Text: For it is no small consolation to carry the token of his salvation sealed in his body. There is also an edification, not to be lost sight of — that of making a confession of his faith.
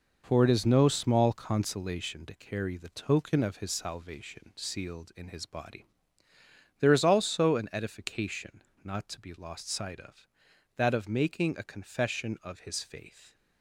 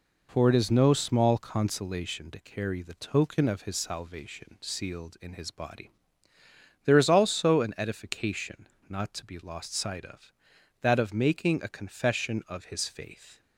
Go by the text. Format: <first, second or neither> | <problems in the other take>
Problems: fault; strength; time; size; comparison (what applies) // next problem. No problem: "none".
second | gets quieter; strong; throughout; 7.5 dB